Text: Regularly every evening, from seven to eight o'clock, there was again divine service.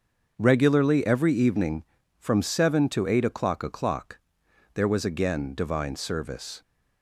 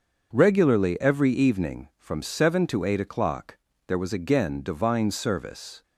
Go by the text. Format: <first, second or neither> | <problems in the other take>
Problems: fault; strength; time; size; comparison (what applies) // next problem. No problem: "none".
second | starts louder than the rest; until 1.3 s; 6.5 dB; also in the second // says "o'clock" twice; at 3.6 s